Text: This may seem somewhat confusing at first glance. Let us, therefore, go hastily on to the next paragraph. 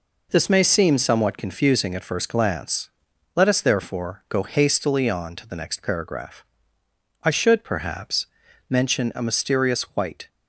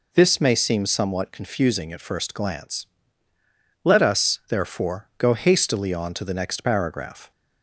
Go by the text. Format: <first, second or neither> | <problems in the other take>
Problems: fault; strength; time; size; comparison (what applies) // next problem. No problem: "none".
second | goes on to say "I should perhaps mention a mysterious white"; strong; from 7.2 s on; 3.0 s long